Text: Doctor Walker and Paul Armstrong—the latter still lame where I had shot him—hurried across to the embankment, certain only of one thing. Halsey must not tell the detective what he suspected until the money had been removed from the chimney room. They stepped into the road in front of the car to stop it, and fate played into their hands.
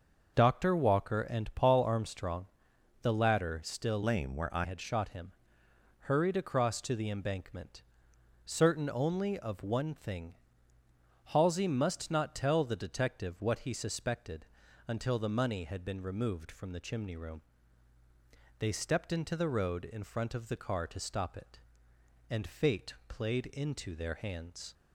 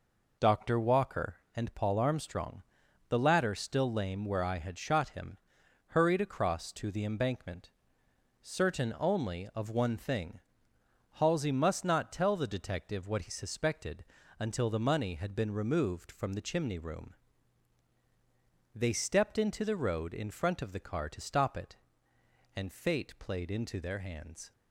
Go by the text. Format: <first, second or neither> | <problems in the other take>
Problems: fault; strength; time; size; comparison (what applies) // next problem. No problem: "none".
second | starts louder than the rest; noticeable; until 1.3 s; 6 dB // changes voice from "lame" to "I"; from 4.0 to 4.6 s; 0.6 s long // pauses between "suspected" and "until"; at 14.4 s; 0.42 s long; slight in the second // pauses between "fate" and "played"; slight; at 22.9 s; 0.16 s long